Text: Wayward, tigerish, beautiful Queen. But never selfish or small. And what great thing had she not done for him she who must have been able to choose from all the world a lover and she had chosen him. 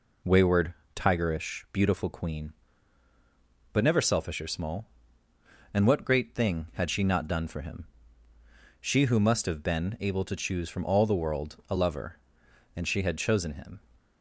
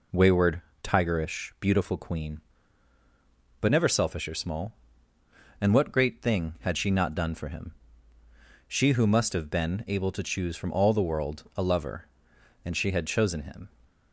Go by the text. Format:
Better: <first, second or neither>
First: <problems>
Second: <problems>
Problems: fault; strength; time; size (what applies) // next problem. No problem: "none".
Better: neither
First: pauses between "him" and "she"; noticeable; at 7.8 s; 0.94 s long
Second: pauses between "him" and "she"; noticeable; at 7.7 s; 0.94 s long